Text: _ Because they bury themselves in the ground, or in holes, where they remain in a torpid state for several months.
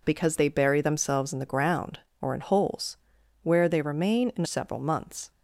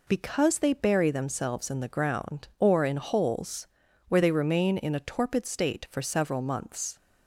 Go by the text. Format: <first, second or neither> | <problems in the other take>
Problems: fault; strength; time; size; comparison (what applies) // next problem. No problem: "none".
second | skips "a torpid state for"; at 4.4 s